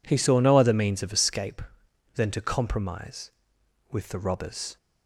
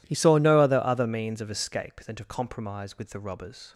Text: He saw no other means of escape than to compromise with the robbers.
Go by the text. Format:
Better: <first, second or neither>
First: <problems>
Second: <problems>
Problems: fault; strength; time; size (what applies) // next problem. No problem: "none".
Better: first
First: none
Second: says "other" twice; at 0.8 s